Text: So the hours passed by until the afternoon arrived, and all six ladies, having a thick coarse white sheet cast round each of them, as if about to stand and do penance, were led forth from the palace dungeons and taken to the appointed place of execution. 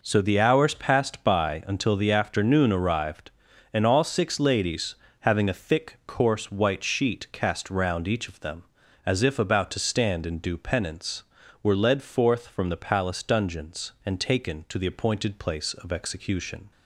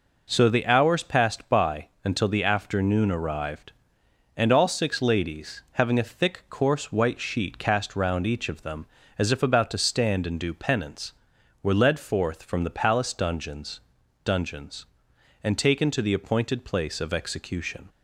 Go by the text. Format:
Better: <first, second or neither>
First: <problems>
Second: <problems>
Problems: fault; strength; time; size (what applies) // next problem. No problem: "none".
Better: first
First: none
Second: pauses between "by" and "until"; slight; at 1.8 s; 0.18 s long // says "dungeons" twice; at 14.2 s